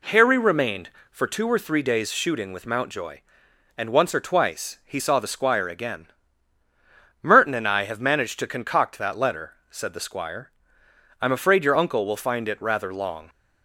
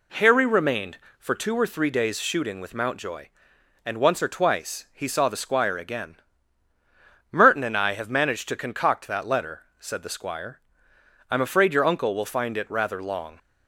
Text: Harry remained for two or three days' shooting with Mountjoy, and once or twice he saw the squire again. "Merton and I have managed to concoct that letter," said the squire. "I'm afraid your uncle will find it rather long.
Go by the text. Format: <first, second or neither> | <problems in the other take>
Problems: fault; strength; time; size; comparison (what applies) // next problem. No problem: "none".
neither | none